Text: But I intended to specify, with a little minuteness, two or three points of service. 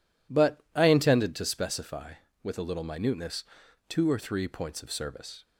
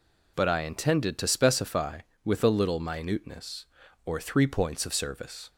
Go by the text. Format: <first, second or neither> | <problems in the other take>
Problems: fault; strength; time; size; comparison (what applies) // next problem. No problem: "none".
first | skips "two"; at 3.8 s